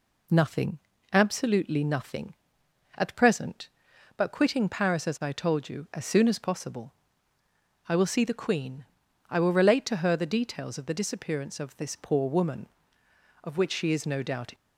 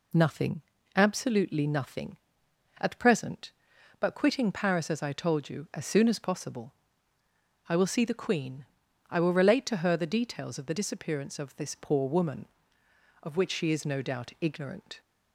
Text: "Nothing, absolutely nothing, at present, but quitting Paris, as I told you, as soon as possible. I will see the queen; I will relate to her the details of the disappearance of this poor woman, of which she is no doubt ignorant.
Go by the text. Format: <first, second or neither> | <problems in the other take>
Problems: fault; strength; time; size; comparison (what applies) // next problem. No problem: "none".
second | stops before "ignorant"; at 14.5 s